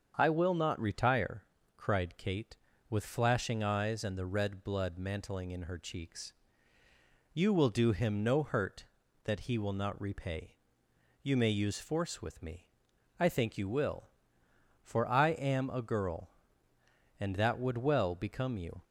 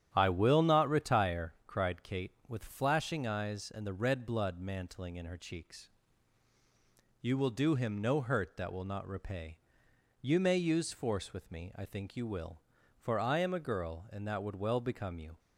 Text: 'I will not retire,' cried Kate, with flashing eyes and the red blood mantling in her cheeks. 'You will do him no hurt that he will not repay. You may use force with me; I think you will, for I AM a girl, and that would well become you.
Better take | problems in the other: first | starts louder than the rest; strong; until 1.1 s; 10 dB; strong in the first // skips "he"; at 8.7 s

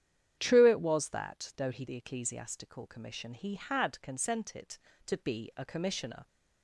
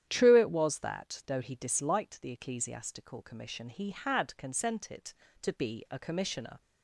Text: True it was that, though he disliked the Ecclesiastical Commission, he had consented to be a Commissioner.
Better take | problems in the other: second | starts louder than the rest; strong; until 1.3 s; 9.5 dB; strong in the second // skips "disliked"; at 1.8 s

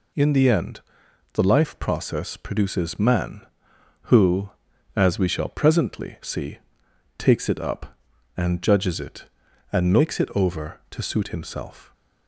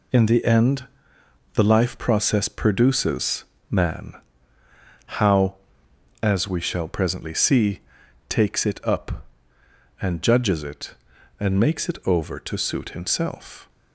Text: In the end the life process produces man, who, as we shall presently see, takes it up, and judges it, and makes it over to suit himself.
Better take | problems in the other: first | pauses between "end" and "the"; noticeable; at 0.8 s; 0.68 s long; noticeable in the first // pauses between "produces" and "man"; slight; at 3.4 s; 0.24 s long // says "how" for "who"; at 5.0 s

